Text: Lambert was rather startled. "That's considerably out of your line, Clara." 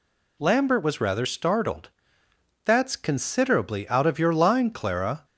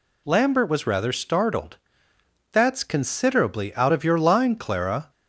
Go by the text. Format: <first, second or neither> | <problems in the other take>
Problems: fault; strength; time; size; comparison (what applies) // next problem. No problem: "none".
neither | none